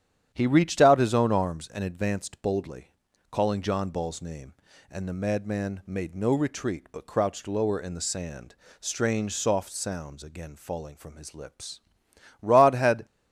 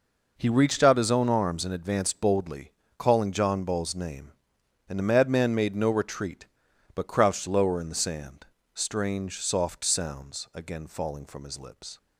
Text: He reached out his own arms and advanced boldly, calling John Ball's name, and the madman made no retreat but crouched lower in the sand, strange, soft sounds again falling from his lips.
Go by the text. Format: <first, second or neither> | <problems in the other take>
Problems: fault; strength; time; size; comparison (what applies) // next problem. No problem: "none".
second | starts louder than the rest; strong; until 1.3 s; 10 dB // goes on to say "Rod had"; noticeable; from 12.4 s on; 0.64 s long